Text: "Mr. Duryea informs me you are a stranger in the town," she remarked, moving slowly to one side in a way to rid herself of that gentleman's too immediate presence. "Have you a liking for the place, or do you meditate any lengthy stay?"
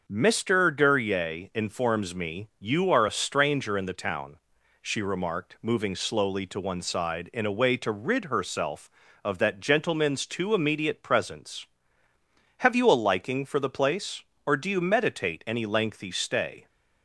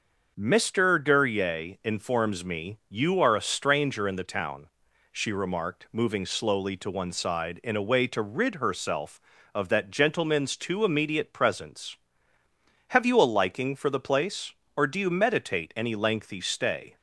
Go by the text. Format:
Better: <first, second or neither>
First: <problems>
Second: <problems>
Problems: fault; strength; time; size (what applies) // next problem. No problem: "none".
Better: neither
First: starts louder than the rest; until 1.0 s; 6 dB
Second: starts louder than the rest; until 1.3 s; 6 dB